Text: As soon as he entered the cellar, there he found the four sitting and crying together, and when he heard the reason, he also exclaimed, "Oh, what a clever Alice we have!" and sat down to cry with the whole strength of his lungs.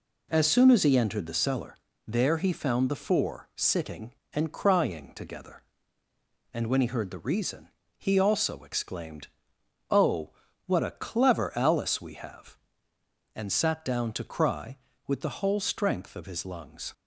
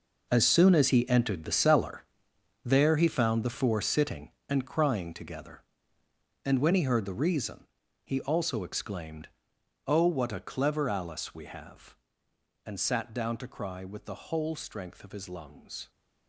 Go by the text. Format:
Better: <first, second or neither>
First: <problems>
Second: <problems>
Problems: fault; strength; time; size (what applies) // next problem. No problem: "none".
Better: first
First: none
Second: gets quieter; strong; throughout; 12.5 dB